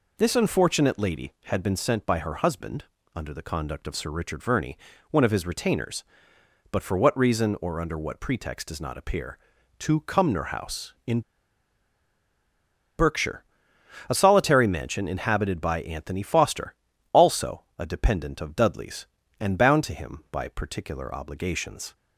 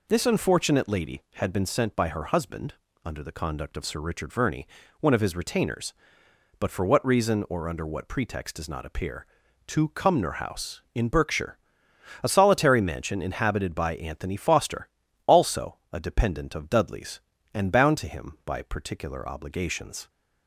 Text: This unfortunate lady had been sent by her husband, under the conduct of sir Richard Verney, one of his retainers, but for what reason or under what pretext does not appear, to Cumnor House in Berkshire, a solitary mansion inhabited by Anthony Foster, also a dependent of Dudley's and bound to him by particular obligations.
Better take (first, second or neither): second